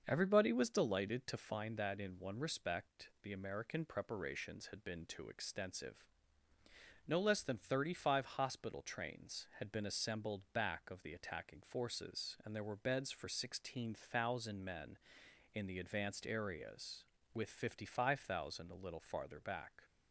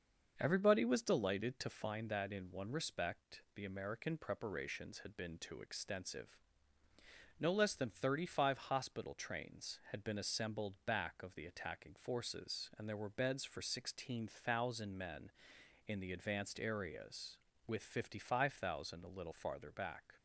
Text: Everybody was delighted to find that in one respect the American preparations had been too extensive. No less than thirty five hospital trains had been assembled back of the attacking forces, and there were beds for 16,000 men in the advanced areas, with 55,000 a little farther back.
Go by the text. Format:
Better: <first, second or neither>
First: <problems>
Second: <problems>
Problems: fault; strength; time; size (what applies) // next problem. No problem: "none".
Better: neither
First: starts louder than the rest; until 1.0 s; 6.5 dB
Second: starts louder than the rest; until 1.3 s; 6.5 dB